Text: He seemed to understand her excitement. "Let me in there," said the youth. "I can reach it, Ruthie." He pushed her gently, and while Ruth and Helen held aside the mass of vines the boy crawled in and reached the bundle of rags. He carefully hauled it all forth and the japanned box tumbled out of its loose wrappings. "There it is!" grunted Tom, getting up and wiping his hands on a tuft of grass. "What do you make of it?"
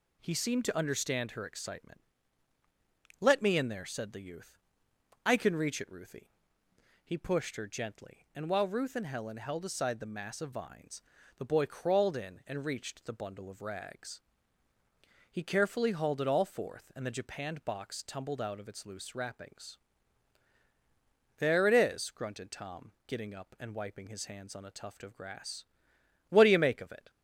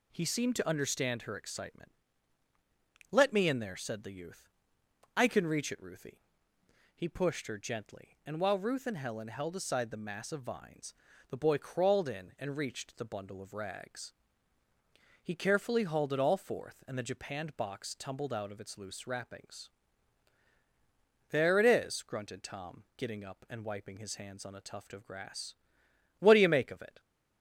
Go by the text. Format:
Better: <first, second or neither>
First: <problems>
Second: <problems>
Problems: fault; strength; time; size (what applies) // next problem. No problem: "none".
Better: neither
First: pauses between "vines" and "the"; slight; at 11.0 s; 0.36 s long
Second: pauses between "vines" and "the"; slight; at 10.9 s; 0.36 s long